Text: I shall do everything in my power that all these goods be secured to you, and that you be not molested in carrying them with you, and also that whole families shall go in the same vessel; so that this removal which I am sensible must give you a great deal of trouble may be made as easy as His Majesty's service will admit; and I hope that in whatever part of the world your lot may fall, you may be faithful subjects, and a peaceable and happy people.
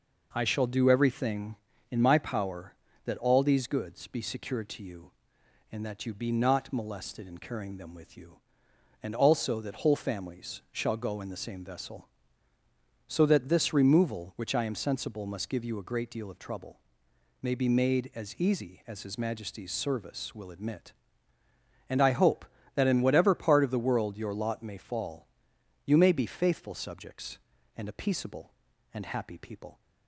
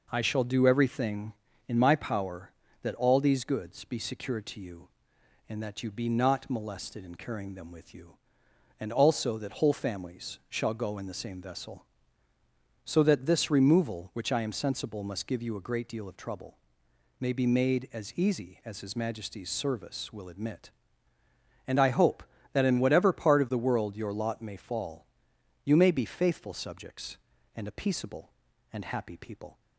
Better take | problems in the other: neither | pauses between "trouble" and "may"; noticeable; the same in both

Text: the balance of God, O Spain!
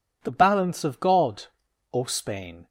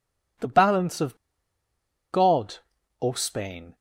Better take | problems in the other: first | pauses between "of" and "God"; noticeable; at 1.1 s; 0.96 s long

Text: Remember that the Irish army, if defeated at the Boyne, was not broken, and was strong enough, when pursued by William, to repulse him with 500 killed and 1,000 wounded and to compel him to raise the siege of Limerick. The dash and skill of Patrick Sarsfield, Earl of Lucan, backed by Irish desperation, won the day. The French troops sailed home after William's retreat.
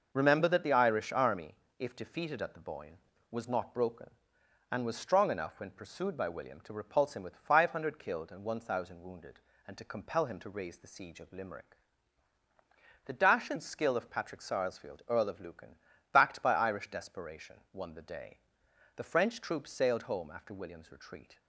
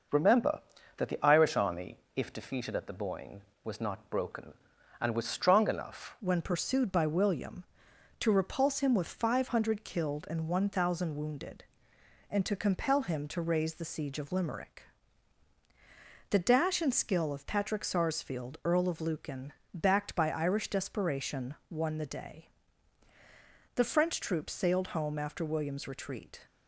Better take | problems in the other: first | changes voice at "when"; from 6.1 s on; 20.3 s long

